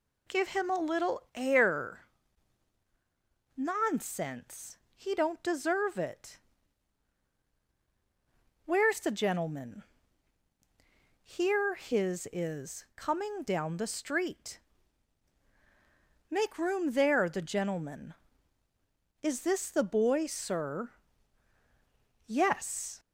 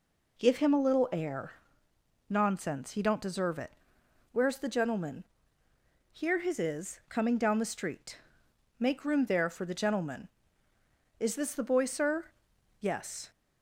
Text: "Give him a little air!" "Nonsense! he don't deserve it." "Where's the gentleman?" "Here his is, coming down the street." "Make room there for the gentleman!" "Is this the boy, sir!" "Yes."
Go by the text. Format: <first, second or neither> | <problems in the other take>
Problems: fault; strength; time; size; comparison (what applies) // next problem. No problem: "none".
second | skips "for"; at 17.2 s